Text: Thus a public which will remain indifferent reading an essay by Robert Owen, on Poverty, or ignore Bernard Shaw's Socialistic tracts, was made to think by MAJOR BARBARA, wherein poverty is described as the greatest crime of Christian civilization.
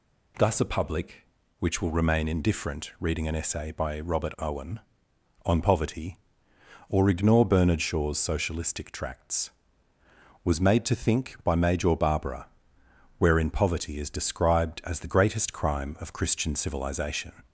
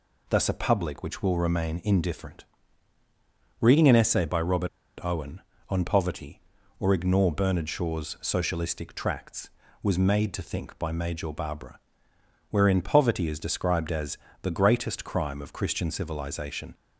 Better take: first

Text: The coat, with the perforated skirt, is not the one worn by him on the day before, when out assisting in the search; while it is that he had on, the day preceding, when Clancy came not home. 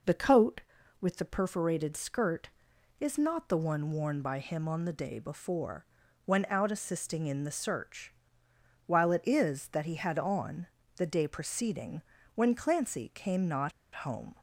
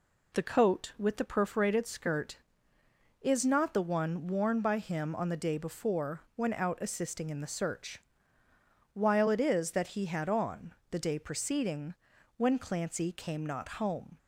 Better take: second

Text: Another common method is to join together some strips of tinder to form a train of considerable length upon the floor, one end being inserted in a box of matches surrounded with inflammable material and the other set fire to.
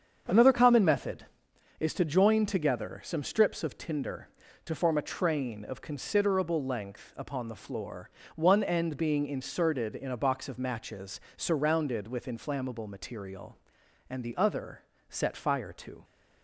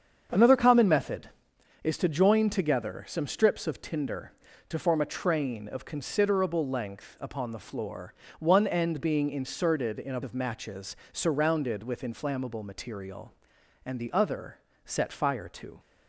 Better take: first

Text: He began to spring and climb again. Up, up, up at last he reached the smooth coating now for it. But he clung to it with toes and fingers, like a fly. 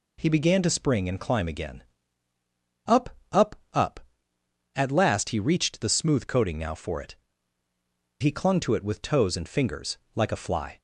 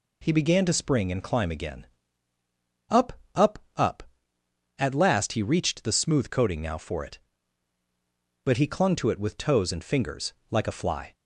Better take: second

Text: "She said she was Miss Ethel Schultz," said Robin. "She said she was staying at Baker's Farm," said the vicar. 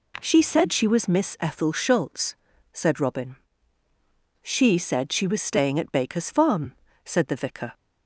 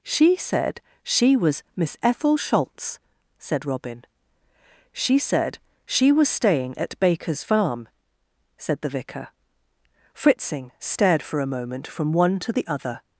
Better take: first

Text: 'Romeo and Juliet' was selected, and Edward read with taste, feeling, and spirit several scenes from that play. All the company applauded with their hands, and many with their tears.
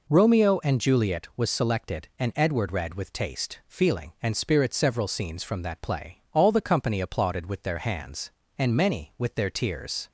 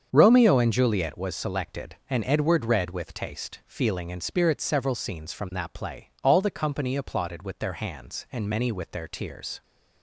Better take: first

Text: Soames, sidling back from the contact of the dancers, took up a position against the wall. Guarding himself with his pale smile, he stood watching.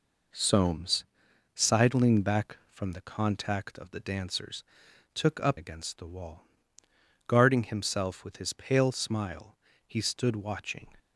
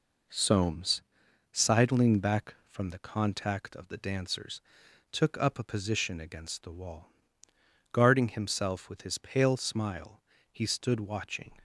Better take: second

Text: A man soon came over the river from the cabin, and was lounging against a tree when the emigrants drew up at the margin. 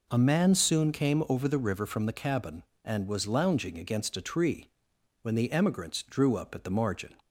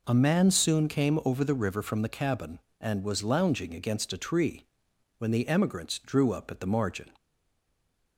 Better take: first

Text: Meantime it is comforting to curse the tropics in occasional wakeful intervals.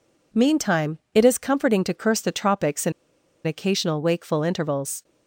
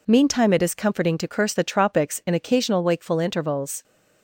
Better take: second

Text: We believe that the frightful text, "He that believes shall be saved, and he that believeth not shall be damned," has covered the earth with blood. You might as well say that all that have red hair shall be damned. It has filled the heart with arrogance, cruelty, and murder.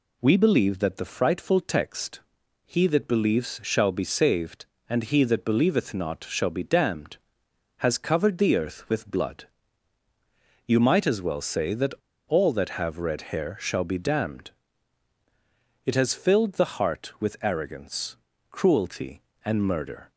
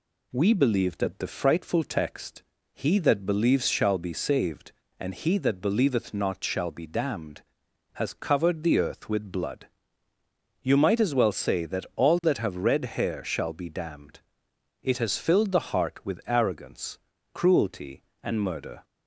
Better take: second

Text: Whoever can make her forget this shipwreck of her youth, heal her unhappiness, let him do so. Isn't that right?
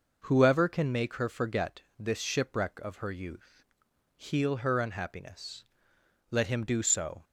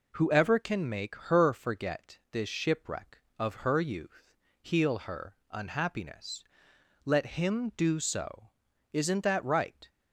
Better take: second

